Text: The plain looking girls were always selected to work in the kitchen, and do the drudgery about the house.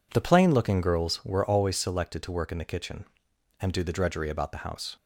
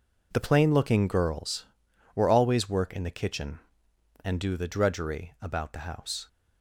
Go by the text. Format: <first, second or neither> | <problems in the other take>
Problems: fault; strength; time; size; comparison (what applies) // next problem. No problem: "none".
first | skips "selected to"; at 2.6 s